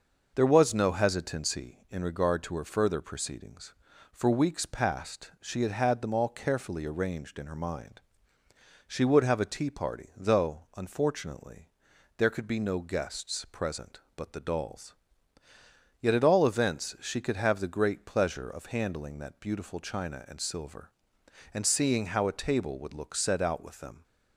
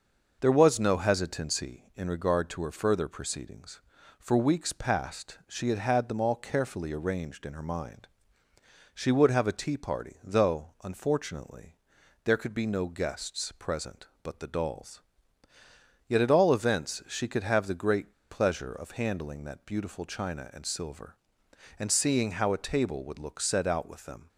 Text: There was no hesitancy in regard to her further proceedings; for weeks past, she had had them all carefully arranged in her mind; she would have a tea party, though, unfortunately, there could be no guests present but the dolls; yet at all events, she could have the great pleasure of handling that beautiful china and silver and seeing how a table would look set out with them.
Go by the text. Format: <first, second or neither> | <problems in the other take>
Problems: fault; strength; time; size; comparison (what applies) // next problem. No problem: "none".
first | starts louder than the rest; noticeable; until 1.4 s; 6 dB; noticeable in the first // pauses between "great" and "pleasure"; slight; at 18.1 s; 0.20 s long